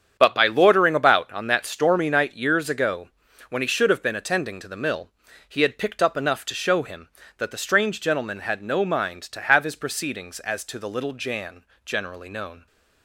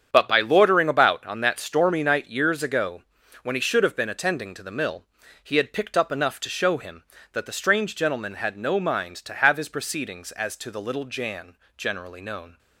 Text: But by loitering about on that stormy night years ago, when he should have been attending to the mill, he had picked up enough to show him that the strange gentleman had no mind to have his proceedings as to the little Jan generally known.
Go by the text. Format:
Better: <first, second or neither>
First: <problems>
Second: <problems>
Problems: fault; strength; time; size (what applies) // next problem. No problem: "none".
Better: neither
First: starts louder than the rest; strong; until 1.2 s; 8 dB // pauses between "Jan" and "generally"; slight; at 11.6 s; 0.20 s long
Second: starts louder than the rest; strong; until 1.1 s; 8 dB // pauses between "Jan" and "generally"; slight; at 11.5 s; 0.20 s long